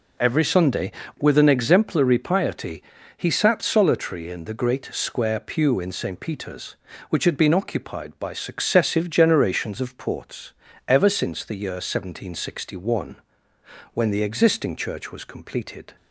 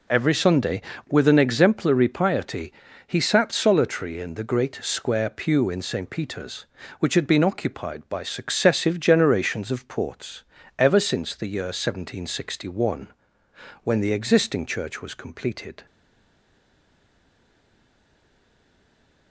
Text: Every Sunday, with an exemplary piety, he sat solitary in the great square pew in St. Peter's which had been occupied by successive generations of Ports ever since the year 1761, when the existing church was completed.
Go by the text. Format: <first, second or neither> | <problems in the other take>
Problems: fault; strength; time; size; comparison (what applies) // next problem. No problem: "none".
first | pauses between "Ports" and "ever"; slight; at 10.4 s; 0.36 s long; slight in the first // stays silent after the last word; strong; from 15.8 s on; 3.5 s long